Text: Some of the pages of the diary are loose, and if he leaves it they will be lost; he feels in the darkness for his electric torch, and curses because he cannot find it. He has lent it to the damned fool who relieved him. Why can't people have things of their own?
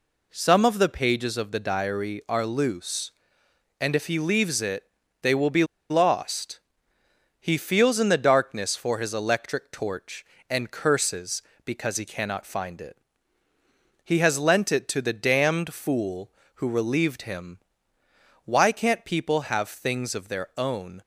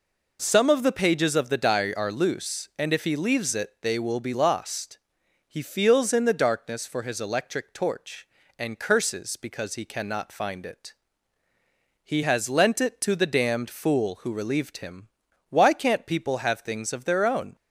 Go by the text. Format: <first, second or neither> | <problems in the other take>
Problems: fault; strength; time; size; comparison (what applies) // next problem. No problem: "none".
second | pauses between "it" and "they"; at 4.8 s; 0.38 s long // pauses between "be" and "lost"; slight; at 5.6 s; 0.26 s long